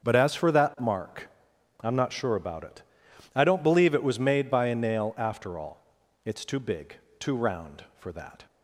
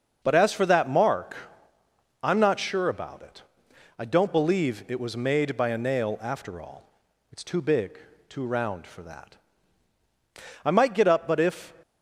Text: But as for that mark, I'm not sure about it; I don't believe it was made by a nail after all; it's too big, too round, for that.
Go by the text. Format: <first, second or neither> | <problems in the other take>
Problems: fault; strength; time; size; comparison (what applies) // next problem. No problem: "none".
first | starts louder than the rest; until 1.2 s; 6 dB; also in the first // goes on to say "I might get up but if"; noticeable; from 10.6 s on; 1.1 s long